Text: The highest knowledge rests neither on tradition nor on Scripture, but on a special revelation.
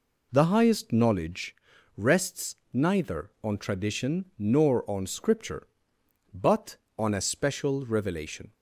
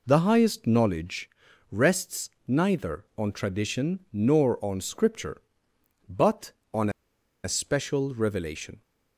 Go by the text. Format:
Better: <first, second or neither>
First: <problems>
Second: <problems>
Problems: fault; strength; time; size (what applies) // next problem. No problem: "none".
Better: first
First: pauses between "knowledge" and "rests"; at 1.5 s; 0.40 s long // pauses between "rests" and "neither"; slight; at 2.5 s; 0.18 s long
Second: pauses between "knowledge" and "rests"; at 1.2 s; 0.40 s long // pauses between "rests" and "neither"; slight; at 2.2 s; 0.18 s long // pauses between "on" and "a"; noticeable; at 6.8 s; 0.54 s long